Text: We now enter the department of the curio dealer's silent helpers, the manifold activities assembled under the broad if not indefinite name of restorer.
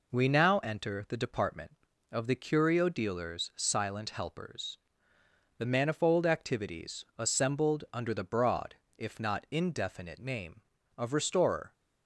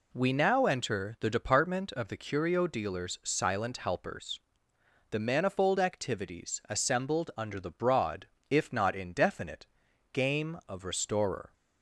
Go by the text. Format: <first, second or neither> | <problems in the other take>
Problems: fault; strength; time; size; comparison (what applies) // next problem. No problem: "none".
first | pauses between "broad" and "if"; slight; at 8.2 s; 0.22 s long; slight in the first // says "game" for "name"; at 10.1 s